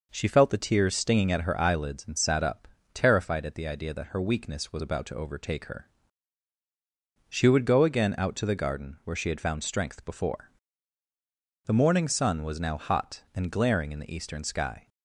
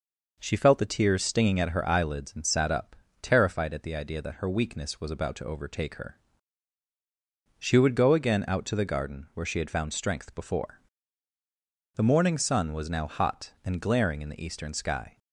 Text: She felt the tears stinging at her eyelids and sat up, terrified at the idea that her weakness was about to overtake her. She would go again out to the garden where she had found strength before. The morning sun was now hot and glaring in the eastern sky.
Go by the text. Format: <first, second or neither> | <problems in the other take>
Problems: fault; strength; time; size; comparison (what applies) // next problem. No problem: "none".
neither | none